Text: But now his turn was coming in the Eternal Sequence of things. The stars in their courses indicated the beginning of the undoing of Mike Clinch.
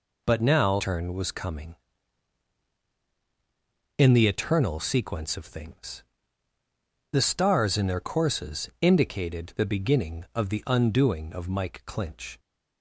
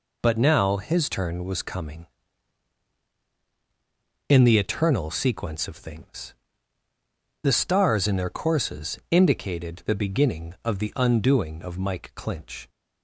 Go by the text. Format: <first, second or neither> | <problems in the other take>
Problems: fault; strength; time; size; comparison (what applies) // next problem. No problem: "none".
second | skips "his"; at 0.7 s